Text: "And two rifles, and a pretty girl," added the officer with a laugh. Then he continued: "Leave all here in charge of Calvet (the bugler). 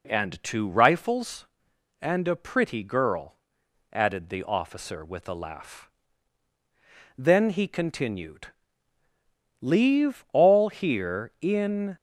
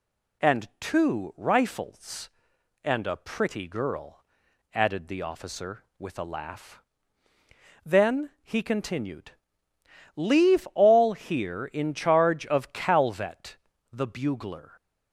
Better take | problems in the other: second | stops before "charge of Calvet the bugler"; at 11.9 s

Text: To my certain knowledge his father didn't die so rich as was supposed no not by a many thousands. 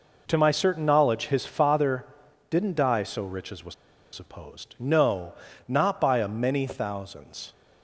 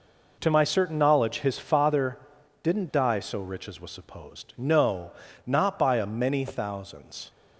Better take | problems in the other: second | pauses between "father" and "didn't"; at 2.0 s; 0.44 s long; also in the second // pauses between "was" and "supposed"; at 3.7 s; 0.39 s long // pauses between "no" and "not"; slight; at 5.3 s; 0.34 s long; slight in the second

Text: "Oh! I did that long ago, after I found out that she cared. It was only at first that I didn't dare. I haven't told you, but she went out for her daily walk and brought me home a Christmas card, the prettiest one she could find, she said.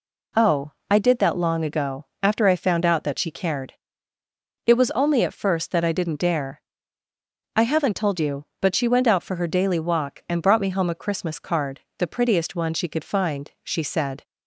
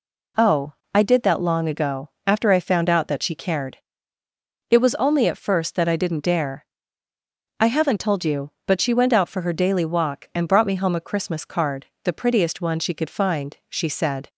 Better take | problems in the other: neither | none

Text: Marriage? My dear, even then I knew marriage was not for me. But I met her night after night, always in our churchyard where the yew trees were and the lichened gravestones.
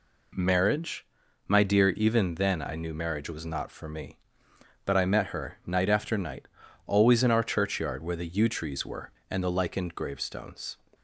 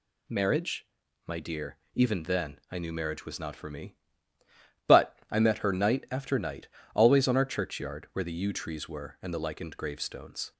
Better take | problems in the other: first | says "on" for "in"; at 7.2 s

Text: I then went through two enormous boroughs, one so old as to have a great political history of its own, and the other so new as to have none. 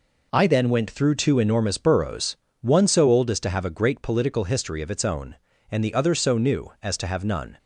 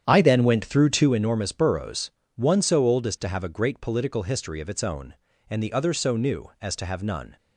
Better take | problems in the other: first | starts louder than the rest; strong; until 1.1 s; 9 dB

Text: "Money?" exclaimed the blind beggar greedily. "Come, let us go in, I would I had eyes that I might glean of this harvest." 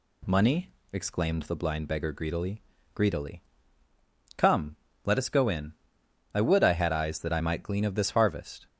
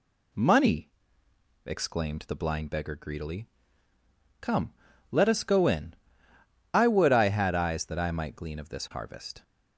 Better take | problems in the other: second | says "greedily" twice; at 2.9 s

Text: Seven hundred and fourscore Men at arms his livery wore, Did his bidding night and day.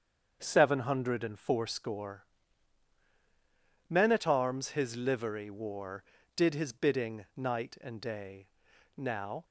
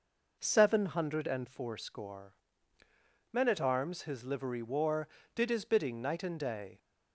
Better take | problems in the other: second | starts louder than the rest; strong; until 1.4 s; 7 dB // pauses between "fourscore" and "Men"; strong; at 2.2 s; 1.6 s long; noticeable in the second // goes on to say "Now"; slight; from 8.9 s on; 0.48 s long

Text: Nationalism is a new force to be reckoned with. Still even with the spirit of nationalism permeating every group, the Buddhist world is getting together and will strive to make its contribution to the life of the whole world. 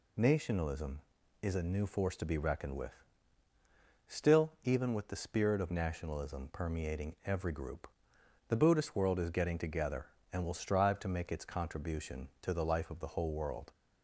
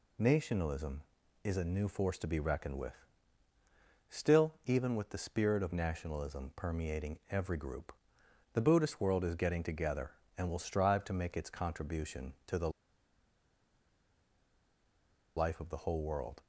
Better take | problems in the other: first | pauses between "the" and "life"; strong; at 12.6 s; 2.6 s long

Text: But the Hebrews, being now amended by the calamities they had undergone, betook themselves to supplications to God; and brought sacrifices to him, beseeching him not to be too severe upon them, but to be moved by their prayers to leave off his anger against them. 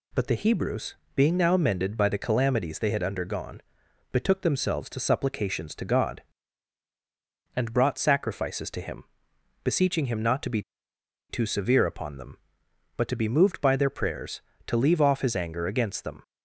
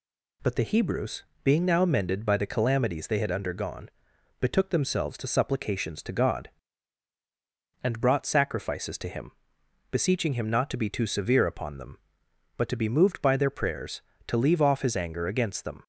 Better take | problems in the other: second | pauses between "be" and "too"; noticeable; at 10.6 s; 0.69 s long

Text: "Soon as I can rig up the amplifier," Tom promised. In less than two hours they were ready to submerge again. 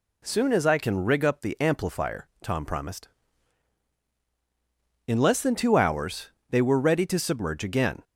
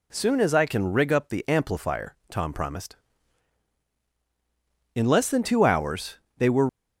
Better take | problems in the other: first | pauses between "hours" and "they"; slight; at 6.1 s; 0.20 s long; slight in the first // stops before "ready to submerge again"; at 6.6 s

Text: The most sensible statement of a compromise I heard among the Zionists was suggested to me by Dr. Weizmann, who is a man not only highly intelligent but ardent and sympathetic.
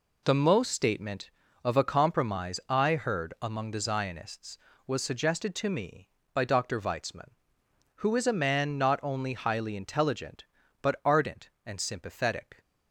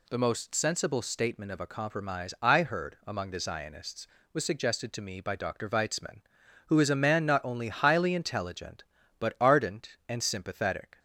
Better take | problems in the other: second | skips "sensible"; at 0.7 s

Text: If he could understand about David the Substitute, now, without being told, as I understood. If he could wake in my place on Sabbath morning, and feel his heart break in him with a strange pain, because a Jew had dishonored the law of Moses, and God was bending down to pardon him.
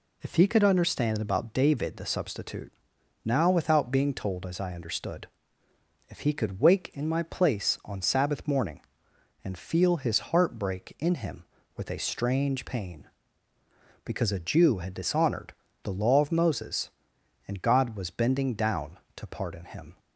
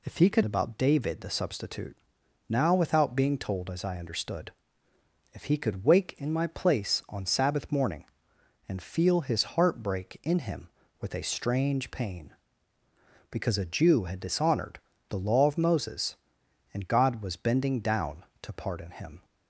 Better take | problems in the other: first | skips "understand"; at 0.4 s // pauses between "dishonored" and "the"; slight; at 14.7 s; 0.30 s long; slight in the first

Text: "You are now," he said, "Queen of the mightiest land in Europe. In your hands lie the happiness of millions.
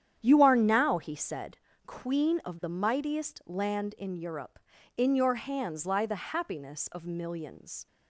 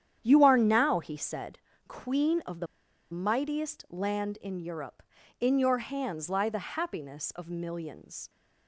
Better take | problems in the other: first | starts louder than the rest; strong; until 1.2 s; 9.5 dB; strong in the first // pauses between "the" and "mightiest"; at 2.6 s; 0.45 s long

